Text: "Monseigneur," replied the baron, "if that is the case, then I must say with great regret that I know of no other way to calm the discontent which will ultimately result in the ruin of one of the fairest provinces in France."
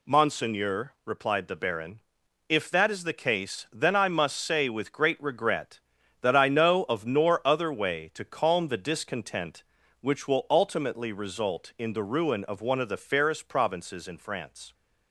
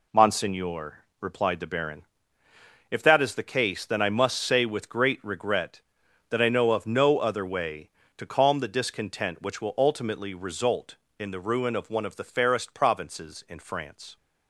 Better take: second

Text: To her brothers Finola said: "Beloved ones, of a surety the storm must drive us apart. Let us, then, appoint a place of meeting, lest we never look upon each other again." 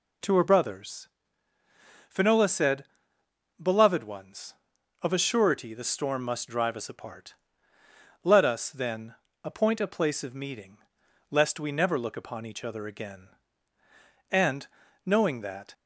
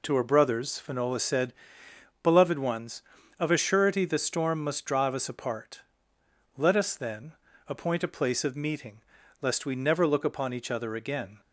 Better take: second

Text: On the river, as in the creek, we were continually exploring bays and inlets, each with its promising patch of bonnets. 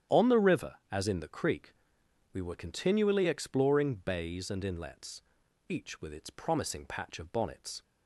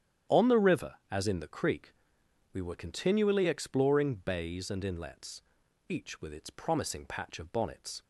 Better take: neither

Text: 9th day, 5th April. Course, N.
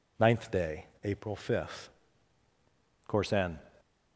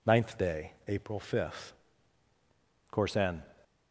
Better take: neither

